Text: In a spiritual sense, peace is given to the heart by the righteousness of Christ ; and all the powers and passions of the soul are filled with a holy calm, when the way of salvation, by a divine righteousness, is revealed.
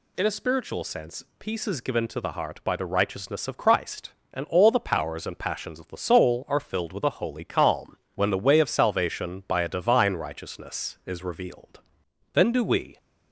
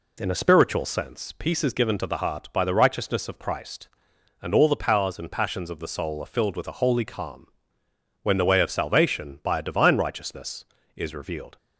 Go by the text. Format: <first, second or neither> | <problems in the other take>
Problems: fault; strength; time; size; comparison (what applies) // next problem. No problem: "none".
second | goes on to say "Then do we"; noticeable; from 12.3 s on; 0.66 s long